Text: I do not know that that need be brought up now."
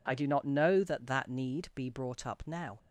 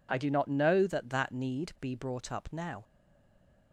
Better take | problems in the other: first | stays silent after the last word; slight; from 2.8 s on; 0.9 s long

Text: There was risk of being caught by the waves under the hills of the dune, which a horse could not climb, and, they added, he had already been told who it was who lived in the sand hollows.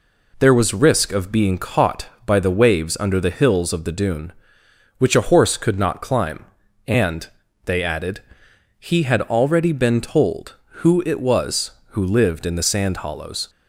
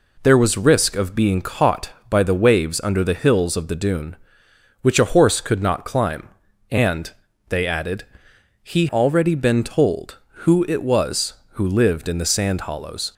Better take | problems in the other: first | skips "had"; at 8.8 s

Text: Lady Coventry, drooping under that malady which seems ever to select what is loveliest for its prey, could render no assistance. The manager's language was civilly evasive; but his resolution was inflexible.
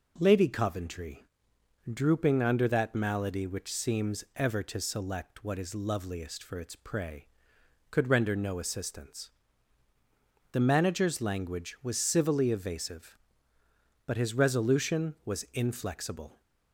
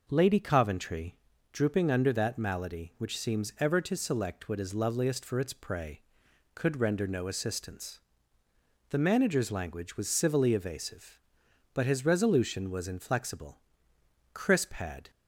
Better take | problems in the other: first | goes on to say "Crisp had"; noticeable; from 14.3 s on; 0.78 s long

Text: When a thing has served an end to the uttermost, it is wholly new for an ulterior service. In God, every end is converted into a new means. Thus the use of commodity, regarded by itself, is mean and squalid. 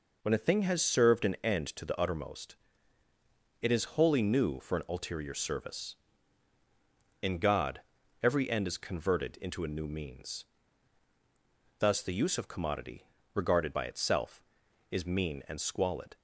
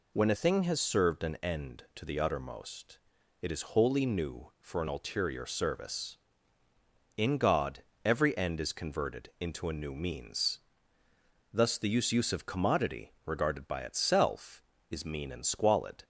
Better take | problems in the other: first | says "use" twice; at 12.1 s

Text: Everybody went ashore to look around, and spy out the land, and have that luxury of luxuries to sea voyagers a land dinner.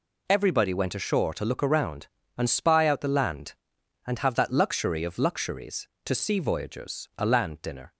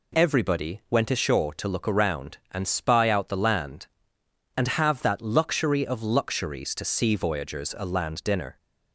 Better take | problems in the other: neither | none

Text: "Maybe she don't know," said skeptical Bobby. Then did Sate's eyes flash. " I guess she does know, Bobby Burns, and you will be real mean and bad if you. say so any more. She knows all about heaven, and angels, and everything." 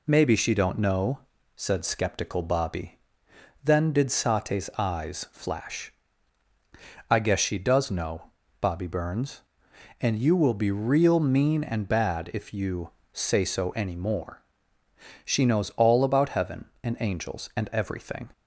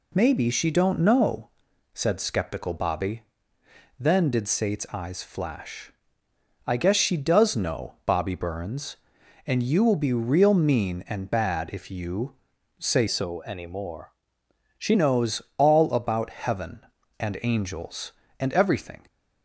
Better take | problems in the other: first | changes voice from "so" to "She"; from 13.0 to 14.9 s; 1.9 s long // pauses between "knows" and "all"; slight; at 15.4 s; 0.16 s long

